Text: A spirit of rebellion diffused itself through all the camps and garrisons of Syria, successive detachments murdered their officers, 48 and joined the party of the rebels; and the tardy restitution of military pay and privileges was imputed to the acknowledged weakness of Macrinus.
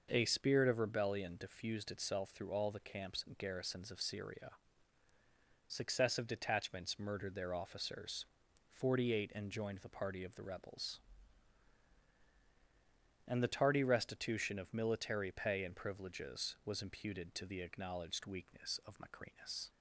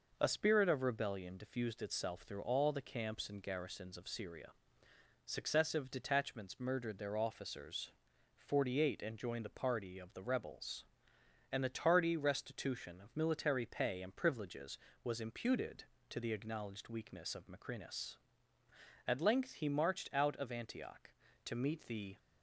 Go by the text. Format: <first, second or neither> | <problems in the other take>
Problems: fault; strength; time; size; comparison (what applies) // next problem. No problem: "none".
first | goes on to say "At length he marched out of Antioch to meet the"; strong; from 19.0 s on; 3.1 s long